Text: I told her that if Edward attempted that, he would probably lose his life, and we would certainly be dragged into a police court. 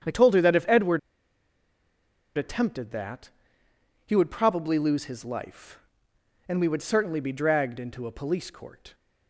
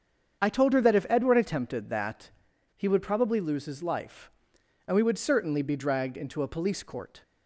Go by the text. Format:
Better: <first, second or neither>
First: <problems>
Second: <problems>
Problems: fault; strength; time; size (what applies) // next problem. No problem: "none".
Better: second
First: starts louder than the rest; strong; until 2.4 s; 8.5 dB // pauses between "Edward" and "attempted"; strong; at 0.9 s; 1.3 s long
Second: starts louder than the rest; strong; until 1.4 s; 7.5 dB